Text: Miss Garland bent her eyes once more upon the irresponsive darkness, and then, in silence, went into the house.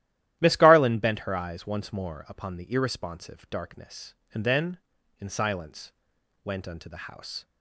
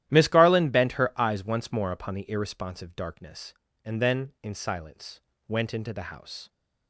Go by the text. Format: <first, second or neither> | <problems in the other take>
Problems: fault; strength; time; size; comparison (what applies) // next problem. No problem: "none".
second | starts louder than the rest; strong; until 1.4 s; 13 dB; strong in the second // says "unto" for "into"; at 6.6 s